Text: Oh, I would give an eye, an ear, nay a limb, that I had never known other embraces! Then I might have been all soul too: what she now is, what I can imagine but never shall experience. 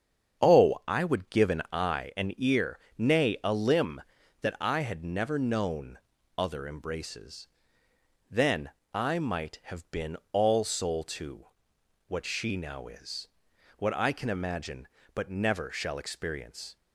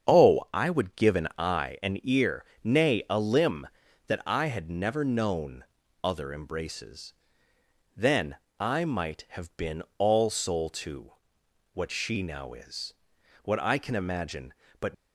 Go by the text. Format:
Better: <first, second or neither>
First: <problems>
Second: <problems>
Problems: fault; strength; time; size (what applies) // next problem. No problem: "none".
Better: first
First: starts louder than the rest; strong; until 1.5 s; 7.5 dB // pauses between "known" and "other"; at 5.9 s; 0.40 s long // pauses between "Then" and "I"; slight; at 8.6 s; 0.24 s long // pauses between "been" and "all"; slight; at 10.1 s; 0.18 s long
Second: starts louder than the rest; strong; until 1.1 s; 7.5 dB // pauses between "known" and "other"; at 5.6 s; 0.40 s long // pauses between "Then" and "I"; slight; at 8.3 s; 0.24 s long // pauses between "been" and "all"; slight; at 9.8 s; 0.18 s long // stops before "never shall experience"; at 14.9 s